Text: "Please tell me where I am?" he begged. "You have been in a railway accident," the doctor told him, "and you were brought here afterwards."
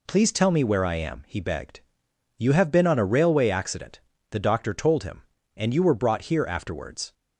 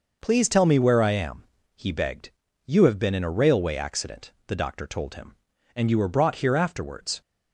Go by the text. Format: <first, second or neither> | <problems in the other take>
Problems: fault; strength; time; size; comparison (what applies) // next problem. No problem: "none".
second | says "on" for "in"; at 2.8 s